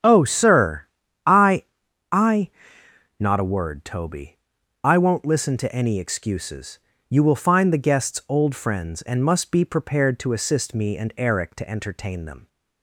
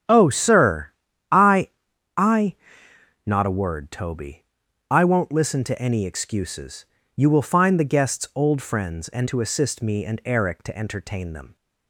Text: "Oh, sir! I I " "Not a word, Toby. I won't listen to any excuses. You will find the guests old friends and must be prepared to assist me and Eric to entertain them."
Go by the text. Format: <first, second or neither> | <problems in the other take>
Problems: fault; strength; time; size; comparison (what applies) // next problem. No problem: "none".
first | starts louder than the rest; strong; until 1.5 s; 9 dB; strong in the first // pauses between "I" and "I"; at 1.7 s; 0.44 s long; also in the first // skips "must be prepared"; at 9.2 s